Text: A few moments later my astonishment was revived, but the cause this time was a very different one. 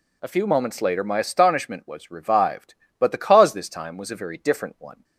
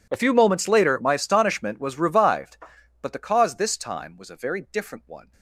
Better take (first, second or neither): first